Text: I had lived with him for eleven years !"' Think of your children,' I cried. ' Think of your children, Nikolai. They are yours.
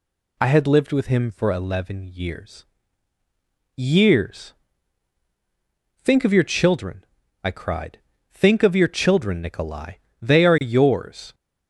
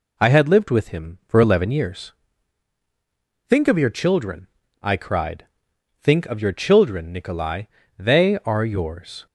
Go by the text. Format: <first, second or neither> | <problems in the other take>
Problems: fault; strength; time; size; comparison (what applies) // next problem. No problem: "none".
second | says "years" twice; at 3.7 s